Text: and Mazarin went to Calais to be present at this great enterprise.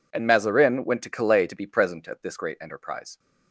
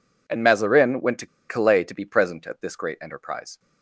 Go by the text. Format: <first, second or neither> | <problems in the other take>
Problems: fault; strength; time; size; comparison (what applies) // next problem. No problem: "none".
first | pauses between "to" and "Calais"; slight; at 1.2 s; 0.22 s long